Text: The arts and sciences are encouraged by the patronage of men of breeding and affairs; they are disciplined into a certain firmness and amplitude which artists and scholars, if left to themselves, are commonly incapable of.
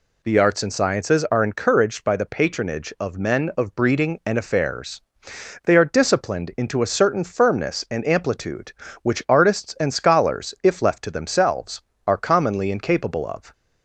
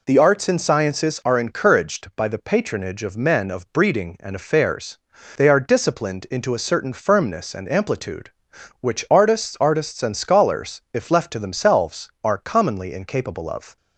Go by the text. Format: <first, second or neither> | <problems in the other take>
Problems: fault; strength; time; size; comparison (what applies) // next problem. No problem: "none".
first | says "artists" twice; at 9.6 s